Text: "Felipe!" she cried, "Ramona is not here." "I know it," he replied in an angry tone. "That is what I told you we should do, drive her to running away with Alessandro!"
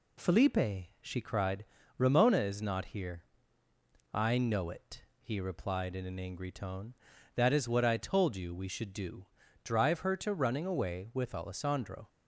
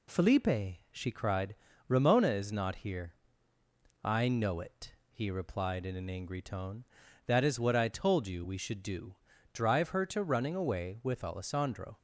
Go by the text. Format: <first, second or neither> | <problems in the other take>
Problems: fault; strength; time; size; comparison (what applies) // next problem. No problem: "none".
neither | none